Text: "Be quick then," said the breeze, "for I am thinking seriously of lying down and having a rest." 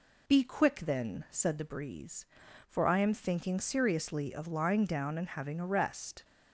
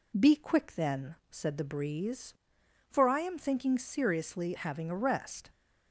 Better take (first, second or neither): first